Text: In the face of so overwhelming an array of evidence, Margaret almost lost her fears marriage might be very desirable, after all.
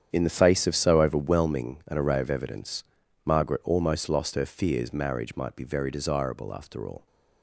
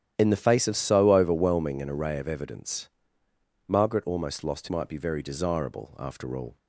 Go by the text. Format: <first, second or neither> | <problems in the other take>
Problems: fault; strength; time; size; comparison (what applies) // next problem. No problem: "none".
first | starts louder than the rest; strong; until 1.1 s; 11 dB; strong in the first // skips "her fears marriage"; at 4.6 s